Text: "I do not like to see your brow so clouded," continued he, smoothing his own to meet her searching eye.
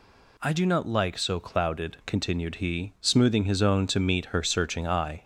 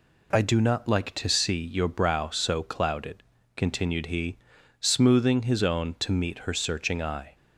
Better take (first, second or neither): second